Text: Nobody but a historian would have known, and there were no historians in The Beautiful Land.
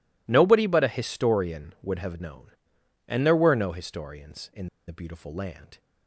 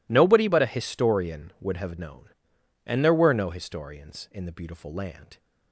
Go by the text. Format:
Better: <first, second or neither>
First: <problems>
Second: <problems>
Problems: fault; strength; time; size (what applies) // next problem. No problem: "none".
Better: second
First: pauses between "in" and "The"; slight; at 4.6 s; 0.21 s long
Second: none